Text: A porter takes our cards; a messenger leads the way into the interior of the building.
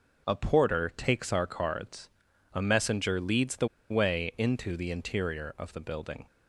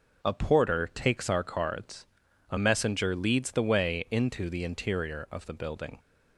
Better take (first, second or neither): second